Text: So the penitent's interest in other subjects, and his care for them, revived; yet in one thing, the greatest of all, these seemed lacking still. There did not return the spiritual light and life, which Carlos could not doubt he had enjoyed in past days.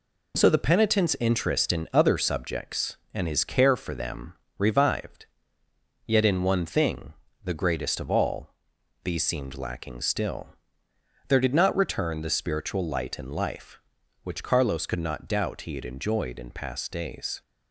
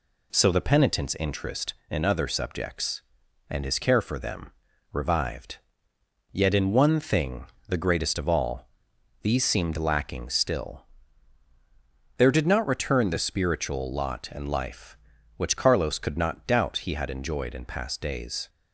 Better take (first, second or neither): first